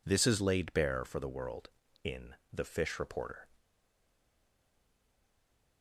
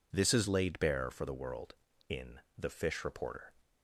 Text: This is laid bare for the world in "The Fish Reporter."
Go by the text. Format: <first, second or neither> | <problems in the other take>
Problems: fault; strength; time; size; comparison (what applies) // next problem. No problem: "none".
second | pauses between "in" and "The"; slight; at 2.3 s; 0.18 s long; slight in the second // stays silent after the last word; from 3.5 s on; 2.3 s long